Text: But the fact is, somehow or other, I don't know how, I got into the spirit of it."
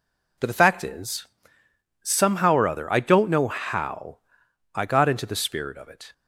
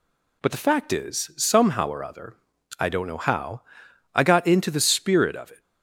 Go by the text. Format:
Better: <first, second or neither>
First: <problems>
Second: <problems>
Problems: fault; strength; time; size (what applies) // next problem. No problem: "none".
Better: neither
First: none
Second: none